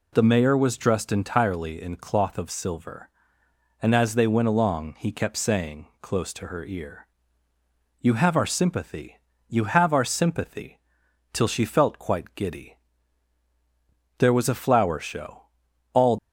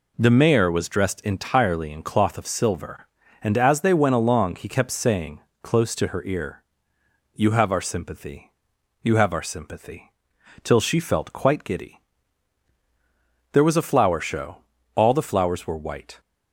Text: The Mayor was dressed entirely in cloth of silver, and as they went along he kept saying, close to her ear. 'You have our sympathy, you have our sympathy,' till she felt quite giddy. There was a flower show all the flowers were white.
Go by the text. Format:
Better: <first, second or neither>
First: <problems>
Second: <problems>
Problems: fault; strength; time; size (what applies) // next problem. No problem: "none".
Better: second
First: pauses between "show" and "all"; noticeable; at 15.3 s; 0.54 s long // stops before "the flowers were white"; at 16.1 s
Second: pauses between "show" and "all"; slight; at 14.5 s; 0.36 s long